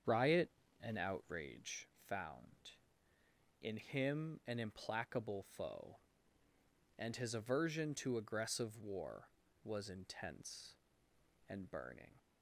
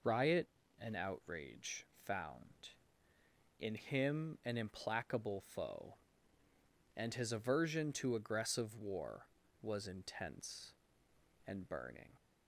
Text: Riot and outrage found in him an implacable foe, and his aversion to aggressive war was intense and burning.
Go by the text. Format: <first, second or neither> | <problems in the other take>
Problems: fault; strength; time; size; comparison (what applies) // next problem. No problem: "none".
second | starts louder than the rest; strong; until 1.7 s; 7.5 dB // pauses between "outrage" and "found"; slight; at 1.8 s; 0.22 s long; slight in the second